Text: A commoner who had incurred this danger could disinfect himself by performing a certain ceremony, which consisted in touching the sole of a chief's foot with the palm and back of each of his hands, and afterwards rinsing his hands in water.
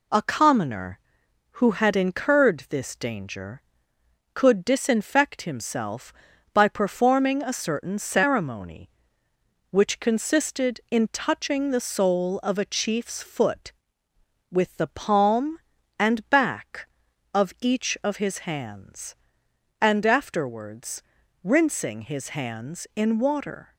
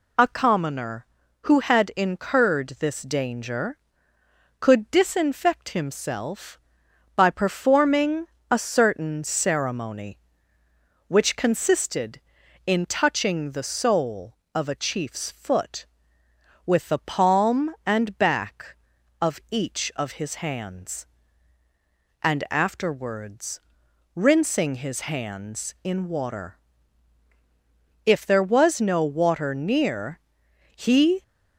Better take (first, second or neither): first